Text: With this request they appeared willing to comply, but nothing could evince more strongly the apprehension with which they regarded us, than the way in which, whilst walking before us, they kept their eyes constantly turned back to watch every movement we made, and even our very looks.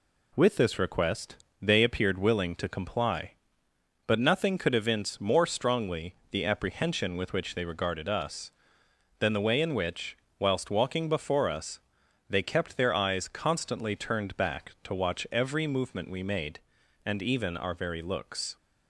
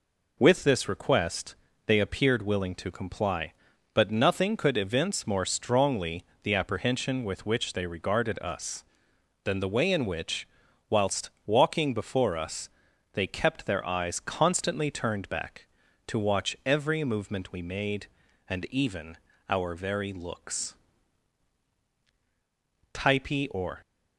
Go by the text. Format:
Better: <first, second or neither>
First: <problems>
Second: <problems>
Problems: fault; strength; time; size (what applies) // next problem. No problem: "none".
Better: first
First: pauses between "request" and "they"; slight; at 1.3 s; 0.26 s long // pauses between "strongly" and "the"; slight; at 6.1 s; 0.16 s long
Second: pauses between "request" and "they"; slight; at 1.5 s; 0.32 s long // pauses between "strongly" and "the"; slight; at 6.2 s; 0.20 s long // pauses between "whilst" and "walking"; slight; at 11.2 s; 0.16 s long // pauses between "even" and "our"; slight; at 19.1 s; 0.32 s long // goes on to say "Typee or"; noticeable; from 22.9 s on; 0.86 s long